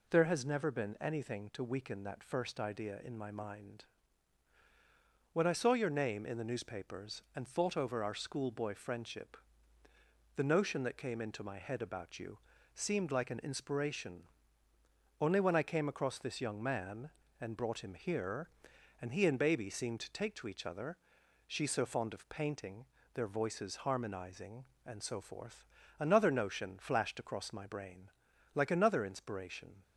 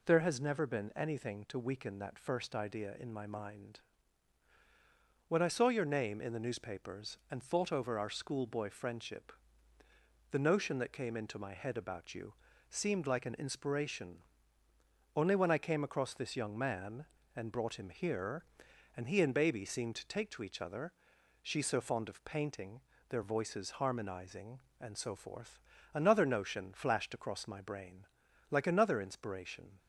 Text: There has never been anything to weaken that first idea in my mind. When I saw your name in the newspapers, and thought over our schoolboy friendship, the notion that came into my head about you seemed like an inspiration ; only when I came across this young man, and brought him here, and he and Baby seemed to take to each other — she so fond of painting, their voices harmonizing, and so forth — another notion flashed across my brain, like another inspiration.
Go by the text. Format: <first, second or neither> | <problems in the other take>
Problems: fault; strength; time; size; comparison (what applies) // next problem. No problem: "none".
neither | pauses between "you" and "seemed"; slight; the same in both